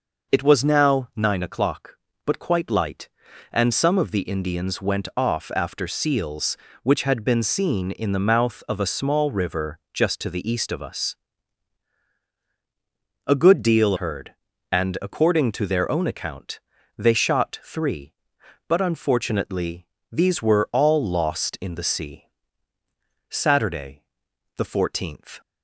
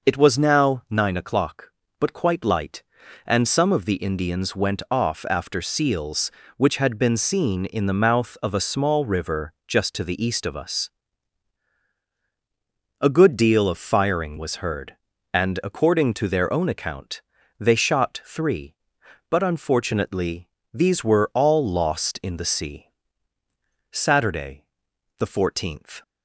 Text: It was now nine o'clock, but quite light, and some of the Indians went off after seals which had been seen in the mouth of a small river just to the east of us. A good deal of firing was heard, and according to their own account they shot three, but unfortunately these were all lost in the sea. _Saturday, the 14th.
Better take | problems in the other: second | skips "of firing was"; at 13.9 s // pauses between "account" and "they"; at 16.6 s; 0.38 s long; also in the second // pauses between "unfortunately" and "these"; slight; at 19.8 s; 0.26 s long; slight in the second

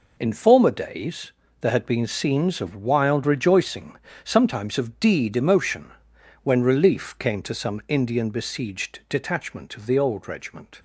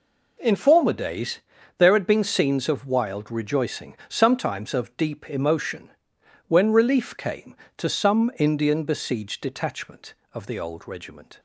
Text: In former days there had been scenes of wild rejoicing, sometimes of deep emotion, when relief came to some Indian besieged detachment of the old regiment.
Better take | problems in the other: second | pauses between "days" and "there"; slight; at 1.3 s; 0.30 s long; also in the second // says "deed" for "deep"; at 4.9 s

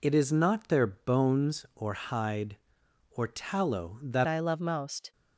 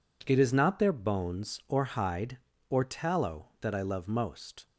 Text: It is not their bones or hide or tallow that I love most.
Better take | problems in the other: second | changes voice at "I"; from 4.2 s on; 0.9 s long

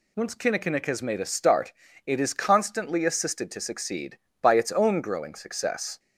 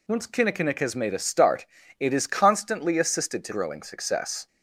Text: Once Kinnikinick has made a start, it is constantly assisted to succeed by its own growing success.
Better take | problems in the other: first | skips "succeed by its own"; at 3.5 s

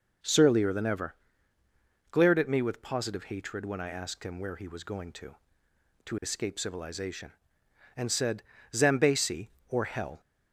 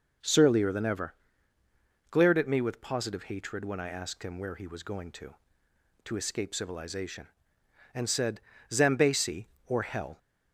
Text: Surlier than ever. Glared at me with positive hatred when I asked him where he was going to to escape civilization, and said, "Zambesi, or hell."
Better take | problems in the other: neither | none

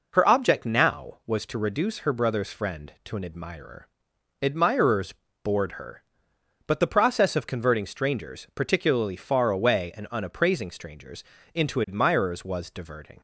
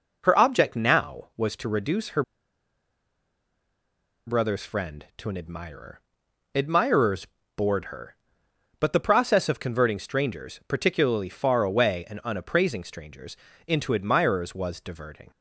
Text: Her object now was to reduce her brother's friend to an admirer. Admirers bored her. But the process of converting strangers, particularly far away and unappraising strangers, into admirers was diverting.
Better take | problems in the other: first | pauses between "her" and "brother's"; strong; at 2.2 s; 2.0 s long // pauses between "Admirers" and "bored"; slight; at 7.2 s; 0.30 s long; slight in the first

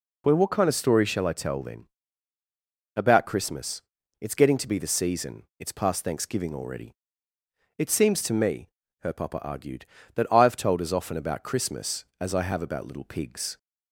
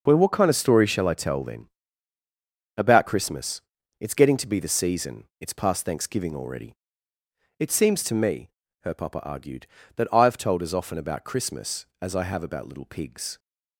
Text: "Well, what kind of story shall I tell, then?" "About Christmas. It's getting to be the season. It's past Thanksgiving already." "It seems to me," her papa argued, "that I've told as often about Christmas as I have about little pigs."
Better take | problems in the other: first | gets quieter; strong; throughout; 11 dB

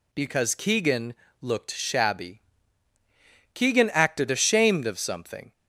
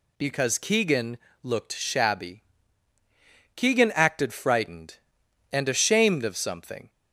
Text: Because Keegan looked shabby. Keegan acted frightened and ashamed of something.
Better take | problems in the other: second | pauses between "Keegan" and "looked"; slight; at 1.1 s; 0.26 s long; slight in the second // skips "frightened and"; at 4.2 s

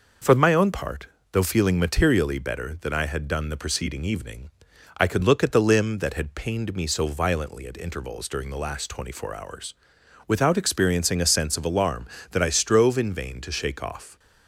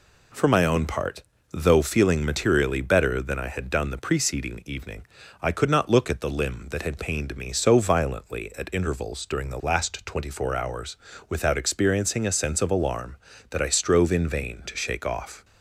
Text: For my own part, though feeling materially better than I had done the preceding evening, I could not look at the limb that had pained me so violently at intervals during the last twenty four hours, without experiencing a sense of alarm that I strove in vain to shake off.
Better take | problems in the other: second | skips "not"; at 5.2 s

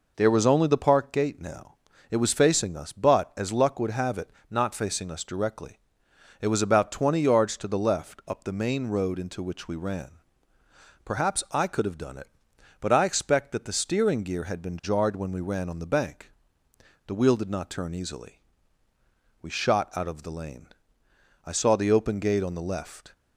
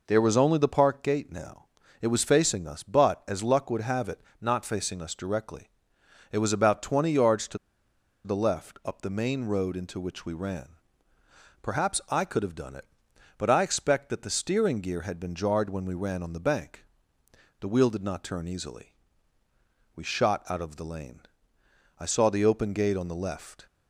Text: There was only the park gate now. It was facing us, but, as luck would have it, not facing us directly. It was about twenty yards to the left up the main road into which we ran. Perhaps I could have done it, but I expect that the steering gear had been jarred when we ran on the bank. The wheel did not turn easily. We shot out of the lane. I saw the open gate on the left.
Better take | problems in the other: first | pauses between "to" and "the"; noticeable; at 7.5 s; 0.67 s long

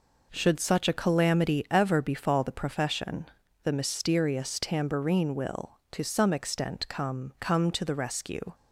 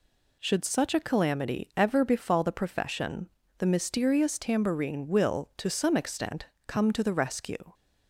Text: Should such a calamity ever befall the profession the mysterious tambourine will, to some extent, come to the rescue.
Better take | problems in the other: second | pauses between "profession" and "the"; slight; at 3.2 s; 0.36 s long; slight in the second // says "come" twice; at 7.4 s

